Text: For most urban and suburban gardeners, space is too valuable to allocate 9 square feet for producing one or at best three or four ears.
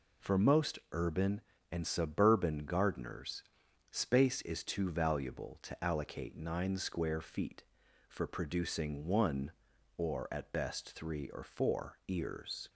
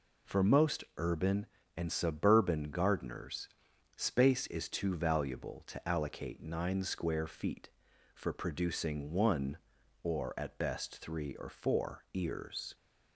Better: neither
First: none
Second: none

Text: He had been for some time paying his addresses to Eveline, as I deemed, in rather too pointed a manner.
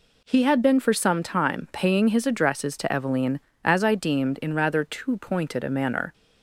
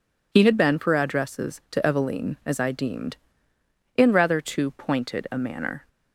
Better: first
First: none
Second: skips "some time paying his"; at 0.9 s

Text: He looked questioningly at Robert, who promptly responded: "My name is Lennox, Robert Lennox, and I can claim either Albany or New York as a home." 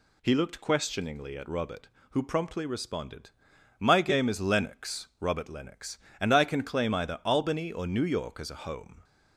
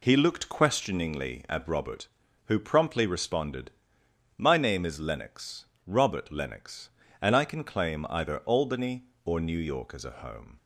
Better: second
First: says "game" for "name"; at 4.0 s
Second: none

